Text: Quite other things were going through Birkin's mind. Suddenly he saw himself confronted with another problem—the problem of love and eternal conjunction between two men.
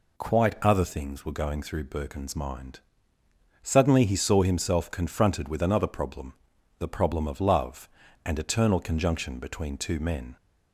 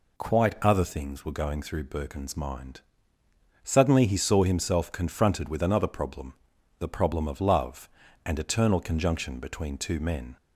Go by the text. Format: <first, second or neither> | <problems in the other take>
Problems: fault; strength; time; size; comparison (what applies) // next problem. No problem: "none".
neither | none